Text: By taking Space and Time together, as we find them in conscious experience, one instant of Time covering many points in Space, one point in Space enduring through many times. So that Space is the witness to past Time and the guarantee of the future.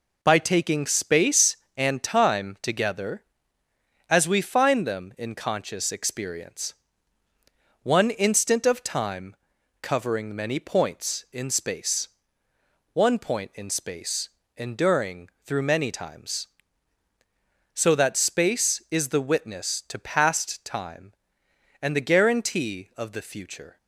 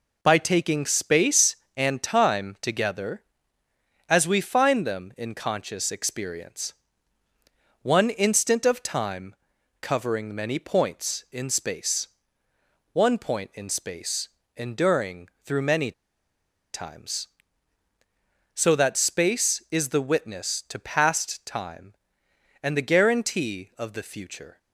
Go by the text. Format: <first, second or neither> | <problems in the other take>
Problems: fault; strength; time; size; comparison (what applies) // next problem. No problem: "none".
first | pauses between "Time" and "covering"; at 9.3 s; 0.44 s long; also in the first // pauses between "Space" and "enduring"; slight; at 14.2 s; 0.30 s long; slight in the first // pauses between "enduring" and "through"; slight; at 15.2 s; 0.16 s long; slight in the first // pauses between "many" and "times"; noticeable; at 15.9 s; 0.82 s long